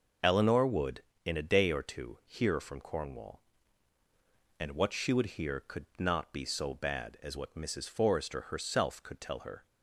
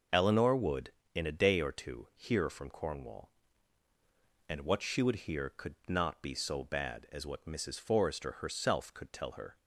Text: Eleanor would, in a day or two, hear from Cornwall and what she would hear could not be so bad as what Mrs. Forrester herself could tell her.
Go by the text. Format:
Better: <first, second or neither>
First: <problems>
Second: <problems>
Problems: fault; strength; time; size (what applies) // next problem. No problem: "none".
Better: neither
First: none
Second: none